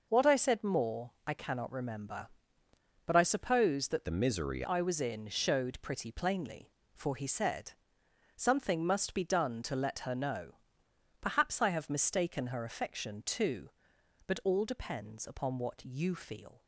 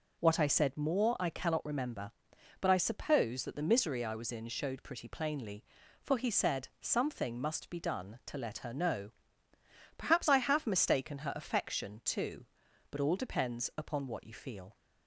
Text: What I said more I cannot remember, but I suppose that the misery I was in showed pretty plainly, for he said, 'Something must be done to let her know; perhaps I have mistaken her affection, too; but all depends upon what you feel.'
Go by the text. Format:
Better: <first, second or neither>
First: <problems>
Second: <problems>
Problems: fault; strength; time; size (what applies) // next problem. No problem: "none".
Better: second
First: pauses between "more" and "I"; slight; at 1.1 s; 0.16 s long // changes voice from "the" to "misery"; from 4.0 to 4.6 s; 0.6 s long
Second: none